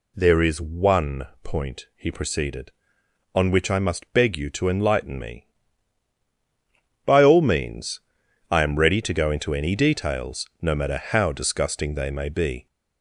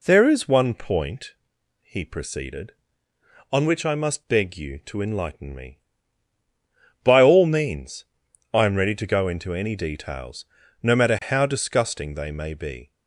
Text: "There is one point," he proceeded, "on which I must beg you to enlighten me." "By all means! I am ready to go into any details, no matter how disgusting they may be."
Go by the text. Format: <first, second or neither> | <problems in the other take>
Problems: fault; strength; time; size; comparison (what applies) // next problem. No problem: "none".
second | gets louder; slight; throughout; 3 dB // pauses between "one" and "point"; slight; at 1.2 s; 0.16 s long